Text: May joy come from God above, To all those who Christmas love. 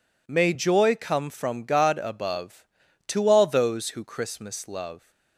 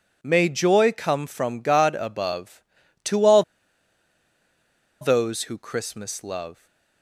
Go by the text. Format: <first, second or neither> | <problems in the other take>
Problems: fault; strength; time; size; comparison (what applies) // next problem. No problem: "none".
first | pauses between "all" and "those"; strong; at 3.4 s; 1.5 s long